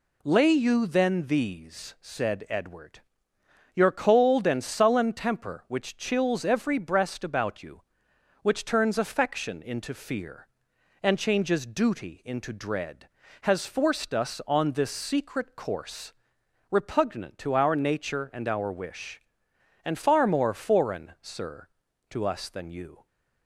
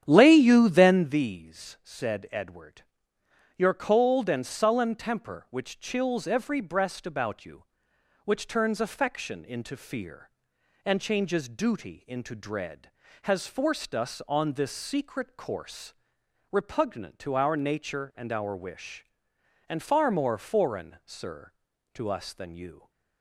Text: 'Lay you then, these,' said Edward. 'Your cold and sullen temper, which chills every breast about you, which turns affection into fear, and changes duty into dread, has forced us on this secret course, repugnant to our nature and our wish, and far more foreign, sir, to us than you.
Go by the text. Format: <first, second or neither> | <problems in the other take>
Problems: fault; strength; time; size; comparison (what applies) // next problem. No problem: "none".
first | starts louder than the rest; strong; until 1.2 s; 9.5 dB